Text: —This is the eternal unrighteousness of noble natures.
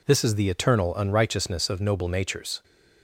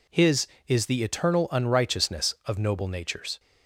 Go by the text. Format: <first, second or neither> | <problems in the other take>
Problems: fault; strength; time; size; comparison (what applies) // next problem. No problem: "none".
first | says "His" for "This"; at 0.0 s